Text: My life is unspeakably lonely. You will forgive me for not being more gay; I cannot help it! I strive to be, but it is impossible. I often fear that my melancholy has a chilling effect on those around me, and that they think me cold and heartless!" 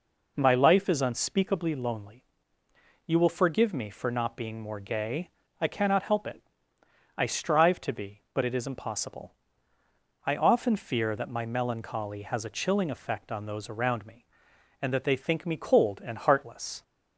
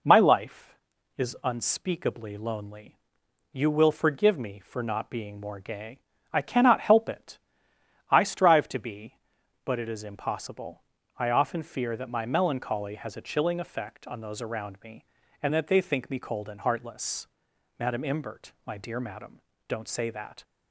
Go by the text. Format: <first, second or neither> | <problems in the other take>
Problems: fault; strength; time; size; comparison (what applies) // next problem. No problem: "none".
first | goes on to say "Madam Imbert my dear Madam don't say that"; strong; from 17.7 s on; 2.6 s long